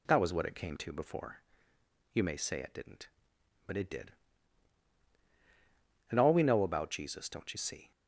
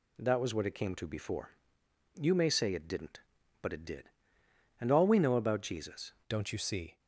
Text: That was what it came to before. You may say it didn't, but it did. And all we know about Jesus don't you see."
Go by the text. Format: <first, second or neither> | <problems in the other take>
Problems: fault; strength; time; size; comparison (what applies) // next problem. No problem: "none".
first | changes voice at "don't"; from 6.2 s on; 0.7 s long